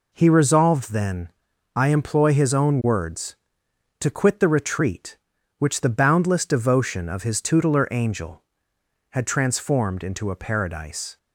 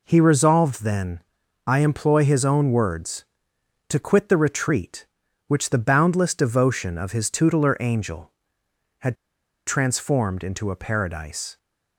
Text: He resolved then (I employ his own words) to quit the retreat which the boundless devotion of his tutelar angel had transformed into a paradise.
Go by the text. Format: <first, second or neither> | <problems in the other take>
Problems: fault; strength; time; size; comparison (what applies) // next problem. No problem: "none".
first | pauses between "had" and "transformed"; noticeable; at 9.1 s; 0.51 s long